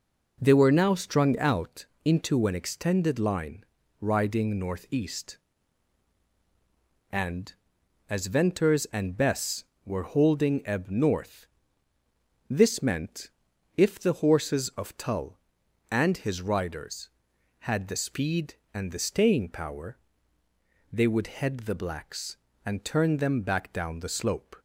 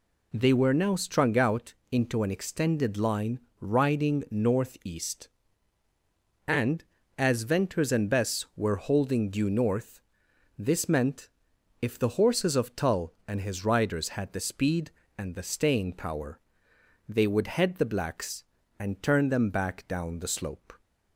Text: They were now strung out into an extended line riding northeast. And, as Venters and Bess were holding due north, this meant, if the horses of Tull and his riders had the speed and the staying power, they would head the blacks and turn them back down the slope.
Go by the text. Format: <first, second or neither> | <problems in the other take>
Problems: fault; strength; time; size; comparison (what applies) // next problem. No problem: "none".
second | pauses between "out" and "into"; slight; at 1.8 s; 0.20 s long; slight in the second // pauses between "line" and "riding"; slight; at 3.6 s; 0.34 s long; slight in the second // says "ebb" for "due"; at 10.6 s